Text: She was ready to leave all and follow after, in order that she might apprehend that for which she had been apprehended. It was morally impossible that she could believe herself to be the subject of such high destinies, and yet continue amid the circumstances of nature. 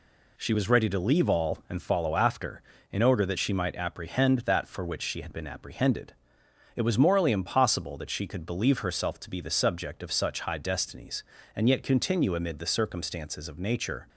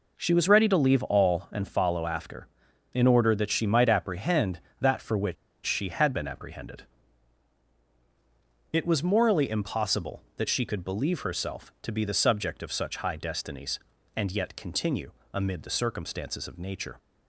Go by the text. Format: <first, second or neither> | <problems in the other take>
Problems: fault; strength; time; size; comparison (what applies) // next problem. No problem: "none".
first | pauses between "which" and "she"; slight; at 5.3 s; 0.30 s long // pauses between "continue" and "amid"; slight; at 15.1 s; 0.22 s long